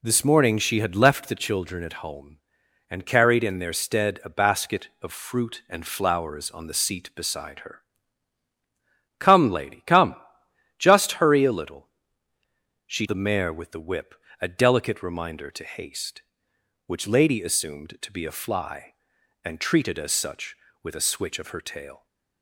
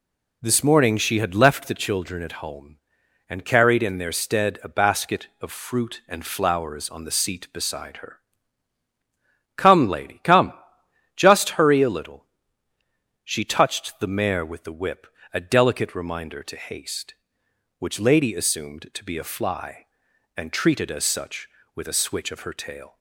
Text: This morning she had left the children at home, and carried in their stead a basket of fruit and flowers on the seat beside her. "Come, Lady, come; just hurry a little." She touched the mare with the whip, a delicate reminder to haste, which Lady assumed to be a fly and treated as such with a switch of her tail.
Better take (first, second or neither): second